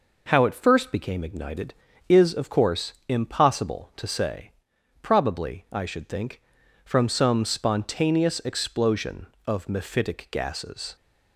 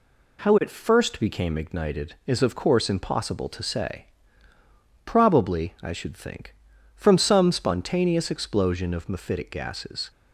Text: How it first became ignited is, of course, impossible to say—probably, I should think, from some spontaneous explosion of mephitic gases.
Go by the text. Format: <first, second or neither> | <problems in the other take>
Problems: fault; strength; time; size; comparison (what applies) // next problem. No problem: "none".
neither | none